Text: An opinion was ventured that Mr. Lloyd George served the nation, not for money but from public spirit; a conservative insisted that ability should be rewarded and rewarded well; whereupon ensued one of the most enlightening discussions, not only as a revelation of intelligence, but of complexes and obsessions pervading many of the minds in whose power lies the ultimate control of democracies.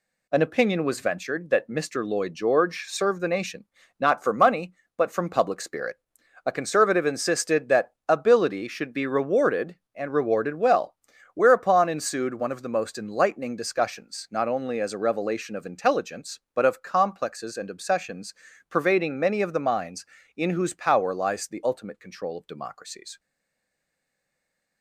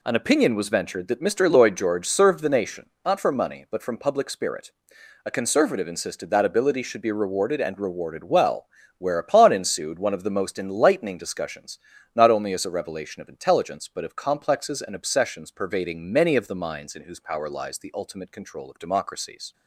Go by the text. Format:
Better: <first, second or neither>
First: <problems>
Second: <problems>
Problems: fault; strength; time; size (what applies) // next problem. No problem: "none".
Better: second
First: pauses between "that" and "ability"; slight; at 7.9 s; 0.16 s long // pauses between "obsessions" and "pervading"; slight; at 18.3 s; 0.34 s long // stays silent after the last word; noticeable; from 23.1 s on; 1.7 s long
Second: none